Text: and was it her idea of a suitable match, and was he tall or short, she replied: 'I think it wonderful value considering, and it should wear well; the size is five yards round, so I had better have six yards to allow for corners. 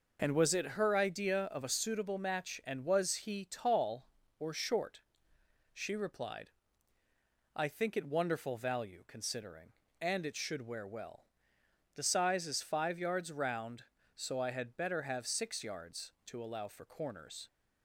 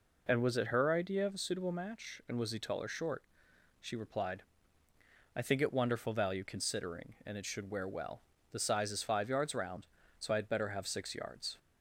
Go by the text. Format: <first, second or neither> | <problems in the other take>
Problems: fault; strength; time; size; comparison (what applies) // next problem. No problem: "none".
first | stops before "to allow for corners"; at 11.5 s